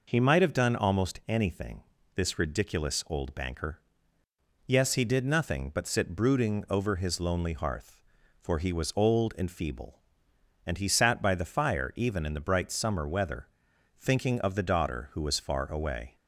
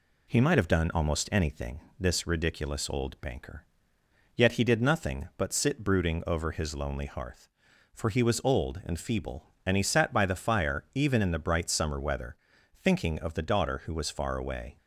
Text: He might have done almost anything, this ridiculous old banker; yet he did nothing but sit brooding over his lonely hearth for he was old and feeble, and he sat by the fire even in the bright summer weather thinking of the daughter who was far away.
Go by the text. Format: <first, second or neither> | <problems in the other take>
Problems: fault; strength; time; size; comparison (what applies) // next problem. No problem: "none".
second | says "yes" for "yet"; at 4.6 s // pauses between "weather" and "thinking"; noticeable; at 13.4 s; 0.52 s long; also in the second